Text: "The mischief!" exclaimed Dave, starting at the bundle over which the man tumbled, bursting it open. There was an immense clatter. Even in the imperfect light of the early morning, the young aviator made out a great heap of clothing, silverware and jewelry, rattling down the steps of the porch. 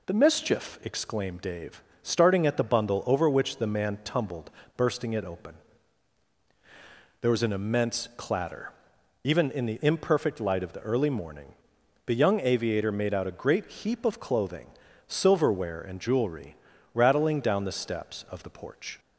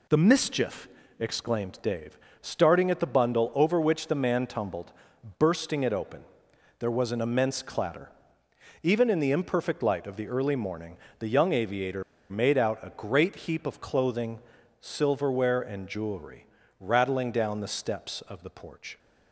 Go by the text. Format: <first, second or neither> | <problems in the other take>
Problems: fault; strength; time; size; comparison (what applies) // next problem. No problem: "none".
first | pauses between "aviator" and "made"; slight; at 12.0 s; 0.26 s long